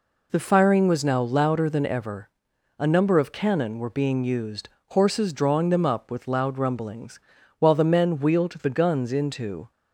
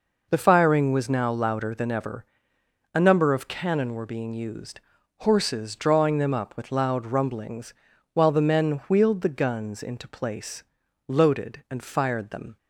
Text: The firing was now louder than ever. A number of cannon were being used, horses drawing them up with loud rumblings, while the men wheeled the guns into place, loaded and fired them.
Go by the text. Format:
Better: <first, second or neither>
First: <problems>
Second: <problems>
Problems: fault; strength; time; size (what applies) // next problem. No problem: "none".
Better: second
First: stops before "place loaded and fired them"; at 9.7 s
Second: none